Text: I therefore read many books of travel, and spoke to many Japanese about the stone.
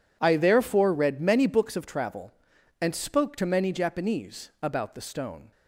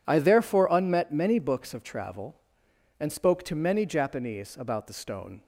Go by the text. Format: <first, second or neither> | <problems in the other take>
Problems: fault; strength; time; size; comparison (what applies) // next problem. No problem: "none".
first | says "unmet" for "read"; at 0.6 s